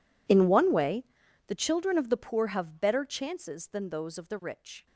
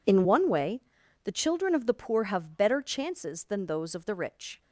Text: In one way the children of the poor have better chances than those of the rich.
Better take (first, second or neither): second